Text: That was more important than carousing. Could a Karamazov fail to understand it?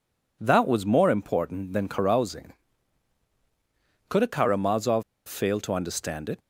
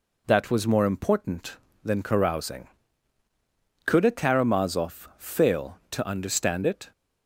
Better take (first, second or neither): second